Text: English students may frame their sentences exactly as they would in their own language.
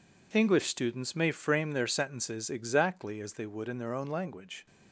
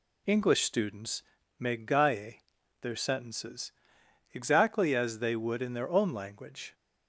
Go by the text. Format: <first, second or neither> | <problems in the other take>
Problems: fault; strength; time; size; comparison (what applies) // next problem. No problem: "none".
first | pauses between "students" and "may"; at 1.2 s; 0.38 s long // says "gaie" for "frame"; at 1.7 s // pauses between "sentences" and "exactly"; noticeable; at 3.7 s; 0.60 s long